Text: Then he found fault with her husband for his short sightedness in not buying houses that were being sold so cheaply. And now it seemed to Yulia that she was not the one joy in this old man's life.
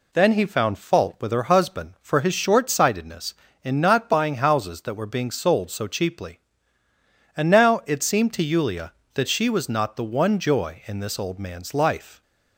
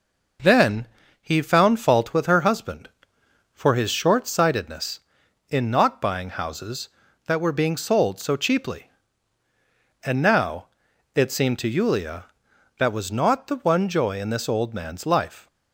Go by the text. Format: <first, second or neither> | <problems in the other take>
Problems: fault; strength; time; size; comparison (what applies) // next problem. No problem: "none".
first | pauses between "Then" and "he"; slight; at 0.8 s; 0.34 s long // pauses between "now" and "it"; noticeable; at 10.6 s; 0.48 s long // skips "she"; at 12.9 s